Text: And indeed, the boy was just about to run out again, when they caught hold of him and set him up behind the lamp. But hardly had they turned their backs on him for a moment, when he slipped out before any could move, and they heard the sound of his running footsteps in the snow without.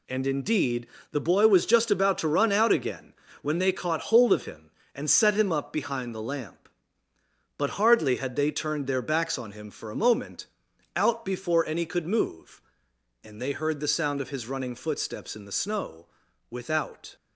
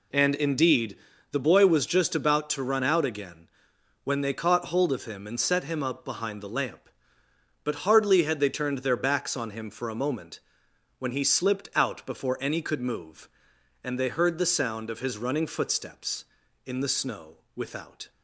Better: second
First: skips "when he slipped"; at 10.7 s // pauses between "snow" and "without"; at 16.0 s; 0.44 s long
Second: pauses between "snow" and "without"; slight; at 17.3 s; 0.18 s long

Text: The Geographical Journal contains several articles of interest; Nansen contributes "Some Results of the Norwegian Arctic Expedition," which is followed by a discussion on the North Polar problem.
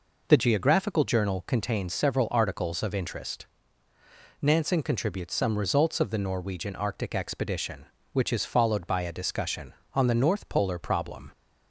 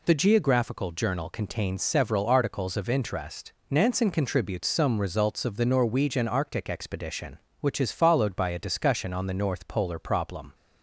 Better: neither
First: none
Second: none

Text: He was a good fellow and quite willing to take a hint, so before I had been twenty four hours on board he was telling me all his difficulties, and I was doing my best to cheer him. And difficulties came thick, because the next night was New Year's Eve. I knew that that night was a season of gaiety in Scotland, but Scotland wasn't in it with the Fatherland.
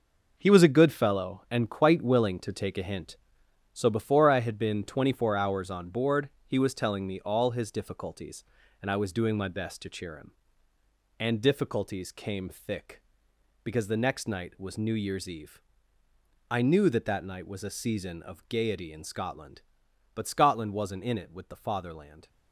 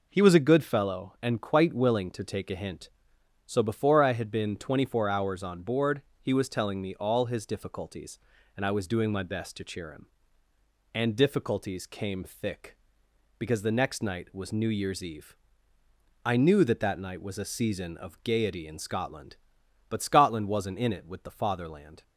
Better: second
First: gets quieter; strong; throughout; 9 dB // pauses between "board" and "he"; slight; at 6.2 s; 0.18 s long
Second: pauses between "board" and "he"; slight; at 6.0 s; 0.20 s long

